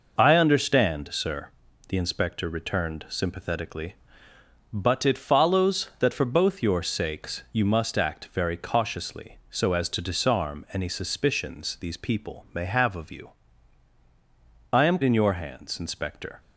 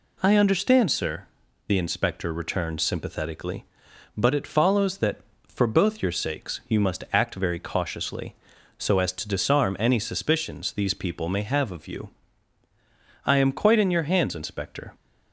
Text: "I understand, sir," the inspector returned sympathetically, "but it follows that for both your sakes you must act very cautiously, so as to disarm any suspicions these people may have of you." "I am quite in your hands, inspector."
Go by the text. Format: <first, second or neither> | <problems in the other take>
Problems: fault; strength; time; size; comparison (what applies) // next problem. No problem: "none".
second | skips "quite"; at 15.0 s